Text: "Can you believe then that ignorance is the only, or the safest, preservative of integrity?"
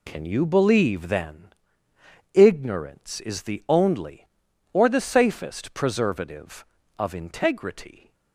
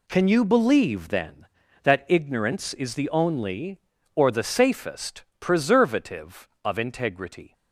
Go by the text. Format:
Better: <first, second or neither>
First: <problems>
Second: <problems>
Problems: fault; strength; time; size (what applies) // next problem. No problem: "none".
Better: second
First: skips "that"; at 1.9 s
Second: none